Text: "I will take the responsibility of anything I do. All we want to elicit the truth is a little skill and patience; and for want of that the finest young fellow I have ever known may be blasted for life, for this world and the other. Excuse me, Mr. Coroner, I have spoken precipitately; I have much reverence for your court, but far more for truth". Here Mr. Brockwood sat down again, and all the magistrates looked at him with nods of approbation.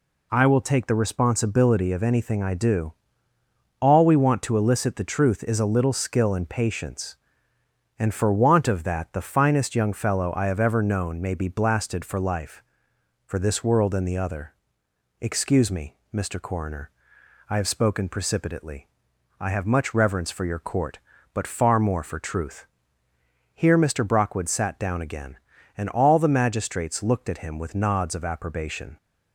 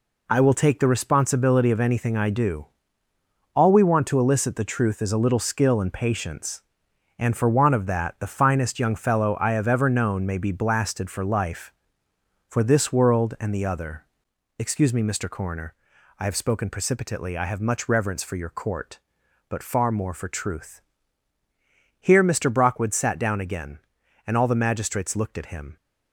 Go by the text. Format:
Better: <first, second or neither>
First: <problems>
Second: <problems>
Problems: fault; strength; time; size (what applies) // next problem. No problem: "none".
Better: first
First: none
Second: stops before "with nods of approbation"; at 25.7 s